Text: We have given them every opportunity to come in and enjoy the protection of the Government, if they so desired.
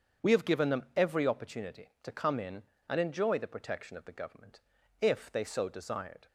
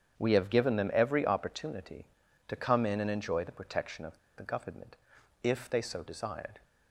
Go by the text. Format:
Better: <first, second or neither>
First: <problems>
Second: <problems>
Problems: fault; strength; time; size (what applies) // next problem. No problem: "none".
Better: first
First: starts louder than the rest; strong; until 1.3 s; 7 dB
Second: starts louder than the rest; strong; until 1.2 s; 8 dB // pauses between "of" and "the"; slight; at 4.1 s; 0.19 s long